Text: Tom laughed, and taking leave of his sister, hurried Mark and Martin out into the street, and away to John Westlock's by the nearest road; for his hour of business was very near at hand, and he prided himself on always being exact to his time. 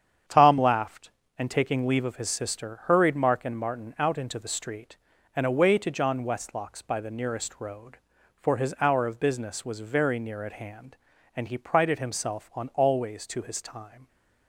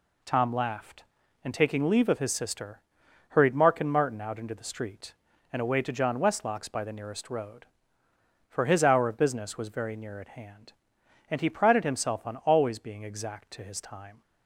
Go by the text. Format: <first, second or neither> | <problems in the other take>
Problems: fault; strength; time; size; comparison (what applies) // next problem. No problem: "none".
second | starts louder than the rest; strong; until 1.5 s; 8.5 dB // skips "being exact"; at 13.2 s